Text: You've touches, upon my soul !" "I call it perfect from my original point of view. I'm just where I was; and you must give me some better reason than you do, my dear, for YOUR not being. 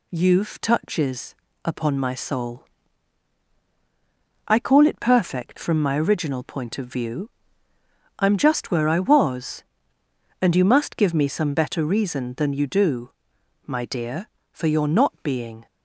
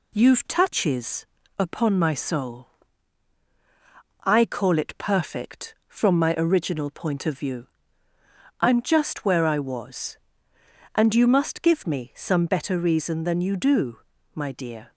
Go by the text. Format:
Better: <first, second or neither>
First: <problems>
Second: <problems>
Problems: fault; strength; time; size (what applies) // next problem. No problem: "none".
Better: first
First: none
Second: stops before "for YOUR not being"; at 14.9 s